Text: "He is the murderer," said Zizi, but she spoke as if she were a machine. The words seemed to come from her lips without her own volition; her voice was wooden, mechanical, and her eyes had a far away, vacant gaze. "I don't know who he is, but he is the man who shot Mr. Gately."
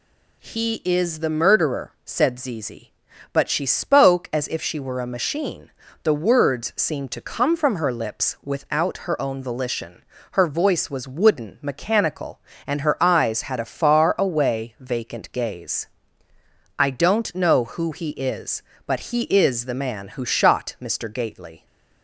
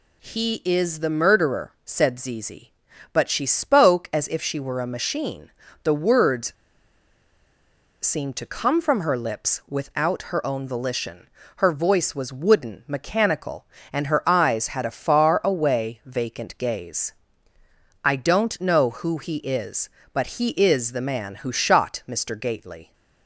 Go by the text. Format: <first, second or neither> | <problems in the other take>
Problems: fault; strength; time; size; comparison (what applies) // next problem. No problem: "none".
first | pauses between "words" and "seemed"; strong; at 6.5 s; 1.5 s long